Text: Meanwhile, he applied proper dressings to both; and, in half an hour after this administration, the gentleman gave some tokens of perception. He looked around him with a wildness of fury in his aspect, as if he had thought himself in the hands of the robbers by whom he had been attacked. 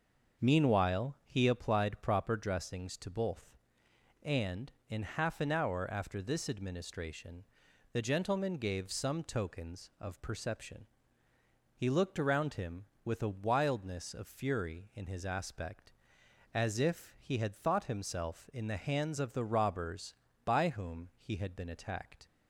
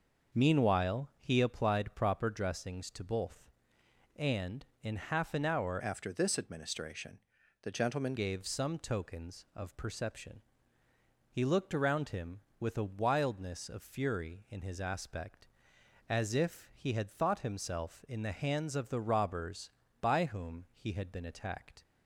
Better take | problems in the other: first | starts louder than the rest; noticeable; until 1.4 s; 6 dB; also in the first // changes voice from "after" to "gentleman"; from 5.7 to 8.1 s; 2.4 s long

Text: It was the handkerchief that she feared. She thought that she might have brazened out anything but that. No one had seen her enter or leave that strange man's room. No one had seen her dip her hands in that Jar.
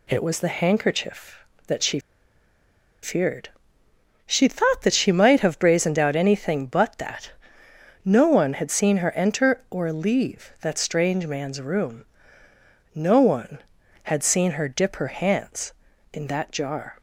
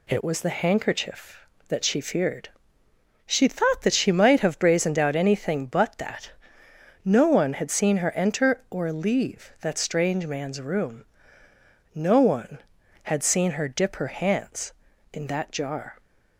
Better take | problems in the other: second | pauses between "she" and "feared"; at 1.9 s; 1.0 s long

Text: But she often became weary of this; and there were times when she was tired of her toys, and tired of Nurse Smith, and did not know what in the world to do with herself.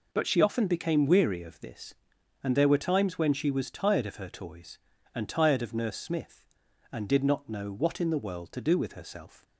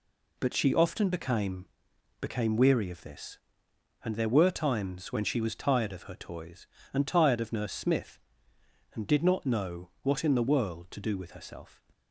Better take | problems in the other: first | says "became" twice; at 2.1 s

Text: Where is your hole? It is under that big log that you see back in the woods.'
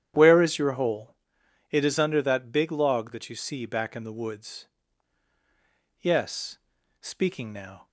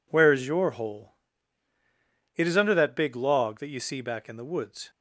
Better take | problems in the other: second | starts louder than the rest; strong; until 1.7 s; 10 dB // goes on to say "Yes speaking now"; strong; from 6.0 s on; 1.8 s long

